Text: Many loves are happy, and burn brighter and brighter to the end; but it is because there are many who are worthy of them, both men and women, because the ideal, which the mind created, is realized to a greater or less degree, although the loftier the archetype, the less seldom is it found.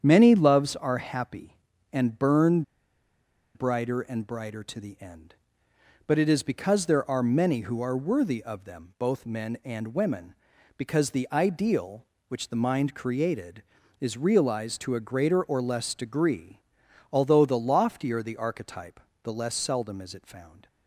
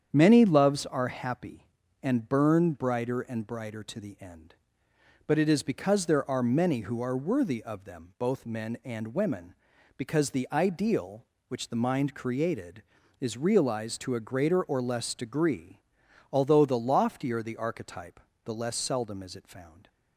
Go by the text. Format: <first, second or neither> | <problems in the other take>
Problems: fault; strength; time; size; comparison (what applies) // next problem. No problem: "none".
second | starts louder than the rest; strong; until 1.0 s; 8 dB; strong in the second // pauses between "burn" and "brighter"; noticeable; at 2.6 s; 0.92 s long